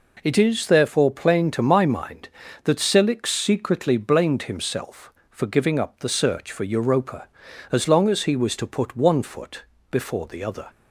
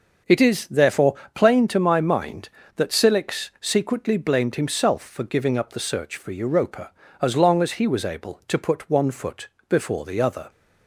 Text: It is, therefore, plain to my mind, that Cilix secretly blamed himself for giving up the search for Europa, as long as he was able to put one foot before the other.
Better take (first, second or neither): second